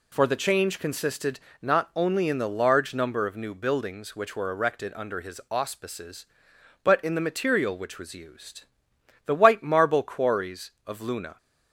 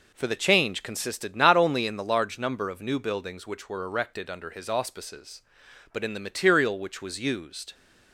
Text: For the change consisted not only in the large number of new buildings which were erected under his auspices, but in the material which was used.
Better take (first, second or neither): second